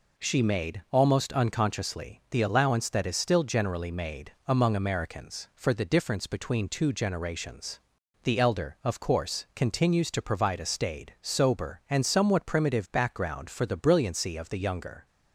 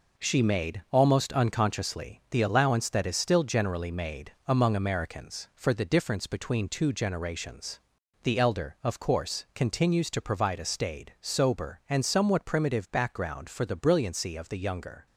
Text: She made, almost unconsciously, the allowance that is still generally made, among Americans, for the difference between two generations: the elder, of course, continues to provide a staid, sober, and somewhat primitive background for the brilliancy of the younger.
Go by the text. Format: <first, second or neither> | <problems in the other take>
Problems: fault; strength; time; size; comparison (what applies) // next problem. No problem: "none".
first | gets quieter; noticeable; throughout; 6 dB